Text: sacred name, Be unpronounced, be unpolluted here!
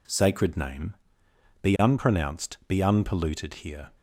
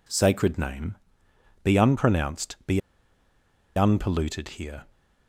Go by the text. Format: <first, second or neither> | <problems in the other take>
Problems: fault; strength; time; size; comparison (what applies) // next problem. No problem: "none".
first | pauses between "be" and "unpolluted"; noticeable; at 2.7 s; 0.96 s long